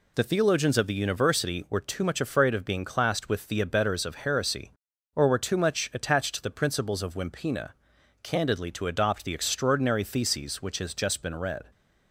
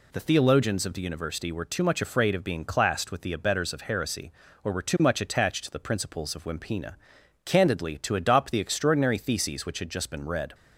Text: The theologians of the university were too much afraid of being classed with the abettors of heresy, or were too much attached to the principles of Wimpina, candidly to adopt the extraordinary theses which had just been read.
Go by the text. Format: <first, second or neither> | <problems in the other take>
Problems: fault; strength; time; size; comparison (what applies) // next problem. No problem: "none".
second | says "has" for "had"; at 10.7 s